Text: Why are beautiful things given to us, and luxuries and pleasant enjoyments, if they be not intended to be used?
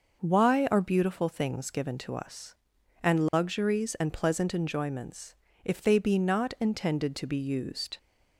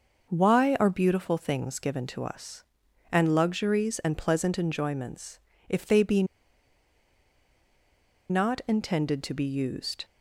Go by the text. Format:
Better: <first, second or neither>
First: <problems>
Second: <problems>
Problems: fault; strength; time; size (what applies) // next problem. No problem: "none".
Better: first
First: starts louder than the rest; noticeable; until 1.2 s; 6 dB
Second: starts louder than the rest; noticeable; until 1.3 s; 6 dB // pauses between "be" and "not"; strong; at 6.2 s; 2.0 s long